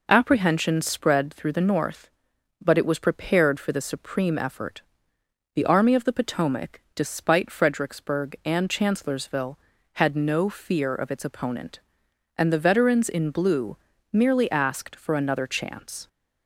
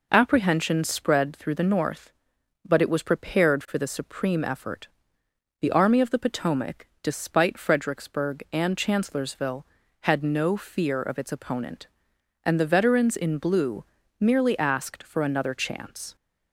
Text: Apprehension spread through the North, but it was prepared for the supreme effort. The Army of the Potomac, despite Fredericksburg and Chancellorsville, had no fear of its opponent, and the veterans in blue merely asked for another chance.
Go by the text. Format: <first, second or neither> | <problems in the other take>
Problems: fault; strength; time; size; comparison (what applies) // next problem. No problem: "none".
neither | pauses between "blue" and "merely"; slight; the same in both